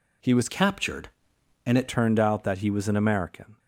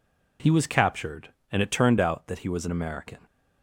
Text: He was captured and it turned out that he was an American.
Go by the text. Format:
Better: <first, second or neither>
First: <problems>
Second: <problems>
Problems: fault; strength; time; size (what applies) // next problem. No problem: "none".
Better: second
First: changes voice from "captured" to "it"; from 0.4 to 1.8 s; 1.4 s long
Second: none